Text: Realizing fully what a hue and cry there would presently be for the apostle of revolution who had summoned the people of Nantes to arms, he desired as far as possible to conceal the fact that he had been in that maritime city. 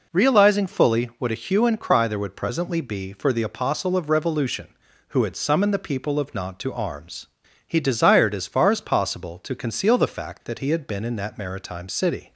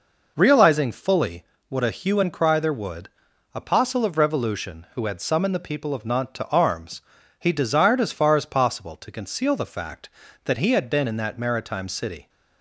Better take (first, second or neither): first